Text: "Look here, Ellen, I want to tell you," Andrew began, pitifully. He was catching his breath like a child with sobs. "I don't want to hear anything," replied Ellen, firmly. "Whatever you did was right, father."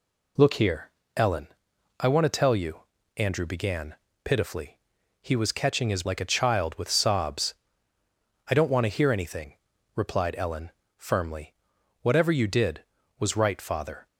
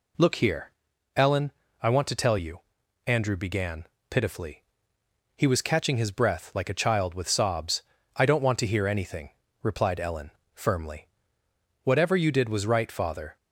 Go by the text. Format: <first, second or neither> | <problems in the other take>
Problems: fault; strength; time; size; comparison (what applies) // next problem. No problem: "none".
second | skips "breath"; at 6.0 s